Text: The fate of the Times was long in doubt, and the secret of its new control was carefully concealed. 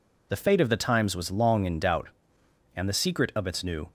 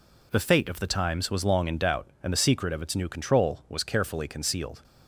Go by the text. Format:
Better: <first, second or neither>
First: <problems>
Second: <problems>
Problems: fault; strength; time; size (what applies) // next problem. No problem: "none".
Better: second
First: stops before "control was carefully concealed"; at 3.8 s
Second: none